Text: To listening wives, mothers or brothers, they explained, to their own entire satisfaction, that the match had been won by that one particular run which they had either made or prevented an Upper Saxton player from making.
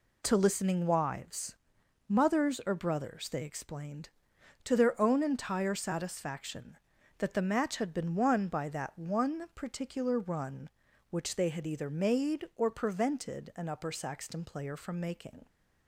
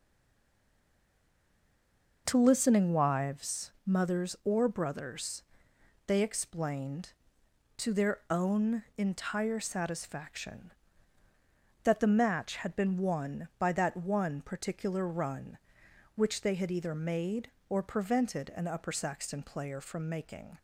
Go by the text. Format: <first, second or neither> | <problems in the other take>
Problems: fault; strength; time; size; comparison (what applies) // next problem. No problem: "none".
first | stays silent before the first word; until 2.2 s; 2.2 s long // pauses between "own" and "entire"; slight; at 8.8 s; 0.16 s long